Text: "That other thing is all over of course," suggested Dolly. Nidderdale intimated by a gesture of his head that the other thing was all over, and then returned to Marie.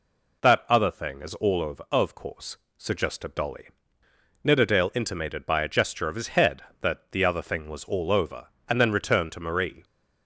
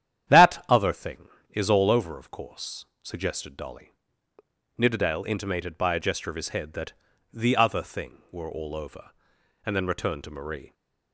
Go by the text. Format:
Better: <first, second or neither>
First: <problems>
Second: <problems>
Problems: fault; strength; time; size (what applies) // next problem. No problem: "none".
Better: first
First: none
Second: starts louder than the rest; strong; until 1.5 s; 10 dB // pauses between "that" and "the"; at 6.9 s; 0.40 s long // says "were" for "was"; at 8.2 s